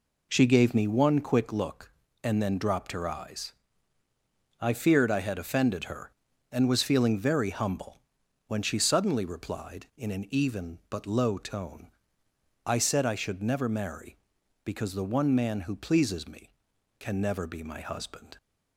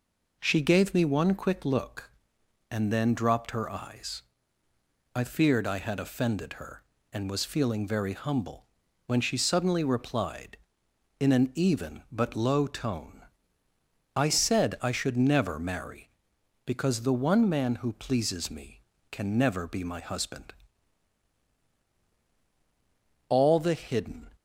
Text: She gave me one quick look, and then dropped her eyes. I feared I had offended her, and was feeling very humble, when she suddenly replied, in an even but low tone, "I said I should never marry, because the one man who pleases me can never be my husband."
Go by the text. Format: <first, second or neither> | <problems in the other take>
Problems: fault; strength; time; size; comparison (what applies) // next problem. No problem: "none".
first | goes on to say "All the hidden"; noticeable; from 23.2 s on; 1.0 s long